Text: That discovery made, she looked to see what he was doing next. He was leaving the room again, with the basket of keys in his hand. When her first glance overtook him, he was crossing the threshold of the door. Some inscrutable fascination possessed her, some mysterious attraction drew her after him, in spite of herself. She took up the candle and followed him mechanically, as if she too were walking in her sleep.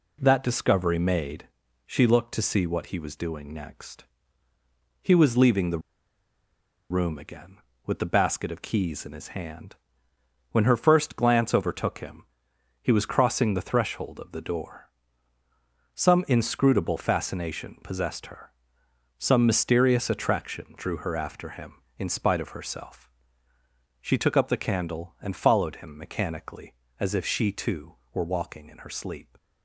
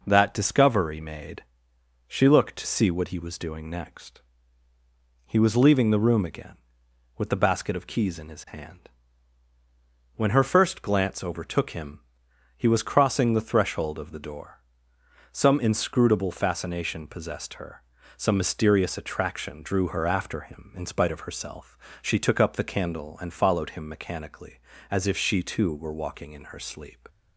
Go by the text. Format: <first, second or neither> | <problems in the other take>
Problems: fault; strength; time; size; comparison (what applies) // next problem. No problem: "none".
second | pauses between "the" and "room"; at 5.7 s; 1.1 s long